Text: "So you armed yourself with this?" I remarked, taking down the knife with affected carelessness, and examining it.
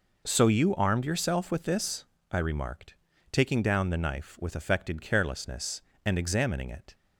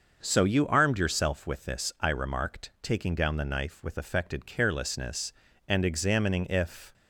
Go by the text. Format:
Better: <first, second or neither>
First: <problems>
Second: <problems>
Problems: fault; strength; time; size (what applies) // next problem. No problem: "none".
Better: first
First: none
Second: starts louder than the rest; until 1.2 s; 6.5 dB // says "if" for "it"; at 6.4 s